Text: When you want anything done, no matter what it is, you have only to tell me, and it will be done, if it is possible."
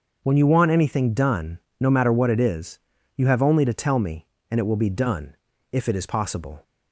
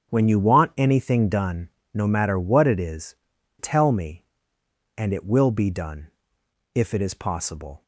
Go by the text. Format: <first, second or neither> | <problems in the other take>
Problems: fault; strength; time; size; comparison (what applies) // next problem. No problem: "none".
first | starts louder than the rest; strong; until 1.1 s; 8 dB; noticeable in the first // skips "you have only to"; at 3.3 s